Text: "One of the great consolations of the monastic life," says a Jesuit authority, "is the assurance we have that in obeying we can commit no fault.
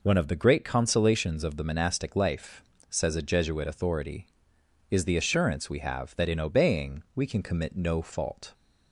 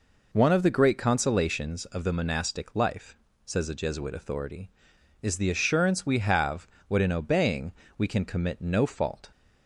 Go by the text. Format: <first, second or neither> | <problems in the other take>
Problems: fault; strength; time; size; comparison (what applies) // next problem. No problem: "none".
first | says "what" for "that"; at 6.8 s // pauses between "obeying" and "we"; slight; at 7.7 s; 0.24 s long